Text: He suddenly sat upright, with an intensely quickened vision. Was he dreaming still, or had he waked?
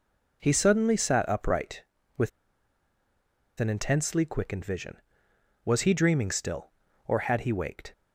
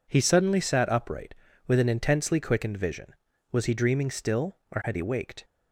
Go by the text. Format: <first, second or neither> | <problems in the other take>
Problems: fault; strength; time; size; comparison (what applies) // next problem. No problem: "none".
second | pauses between "with" and "an"; strong; at 2.2 s; 1.3 s long